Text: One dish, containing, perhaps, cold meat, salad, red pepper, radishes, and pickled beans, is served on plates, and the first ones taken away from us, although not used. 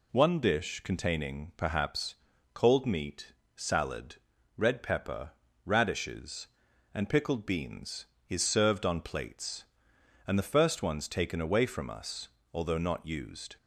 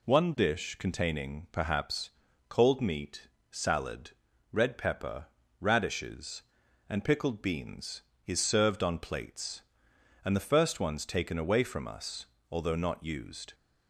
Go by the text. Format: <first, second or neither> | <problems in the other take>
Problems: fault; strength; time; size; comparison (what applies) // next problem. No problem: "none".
neither | none